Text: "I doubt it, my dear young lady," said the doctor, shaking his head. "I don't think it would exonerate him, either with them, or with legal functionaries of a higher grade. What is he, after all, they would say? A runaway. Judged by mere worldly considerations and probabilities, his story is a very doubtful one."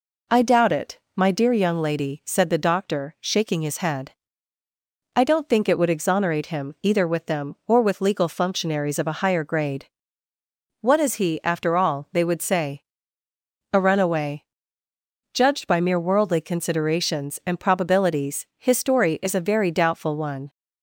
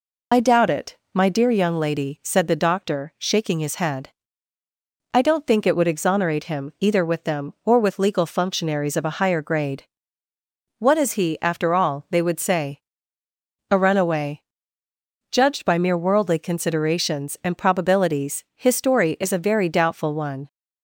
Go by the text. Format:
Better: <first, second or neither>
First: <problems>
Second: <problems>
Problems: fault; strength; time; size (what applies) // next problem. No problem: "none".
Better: first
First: none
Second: loses the start of "I"; at 0.3 s; 40 ms